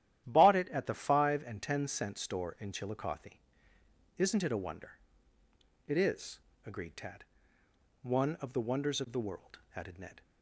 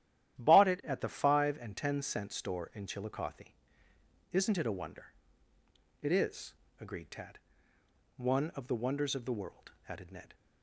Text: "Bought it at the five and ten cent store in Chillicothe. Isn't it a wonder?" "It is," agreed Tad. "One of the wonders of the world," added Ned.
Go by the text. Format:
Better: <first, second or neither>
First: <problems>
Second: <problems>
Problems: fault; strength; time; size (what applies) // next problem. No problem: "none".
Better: neither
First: starts louder than the rest; strong; until 1.2 s; 12 dB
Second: starts louder than the rest; strong; until 1.4 s; 12 dB